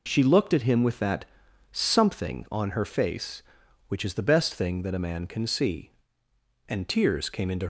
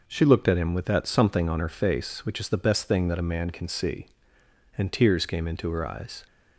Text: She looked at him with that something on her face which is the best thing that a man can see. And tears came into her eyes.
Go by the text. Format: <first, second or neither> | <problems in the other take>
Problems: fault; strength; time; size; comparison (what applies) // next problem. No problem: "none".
second | pauses between "that" and "something"; noticeable; at 1.2 s; 0.48 s long // stops before "her eyes"; at 7.6 s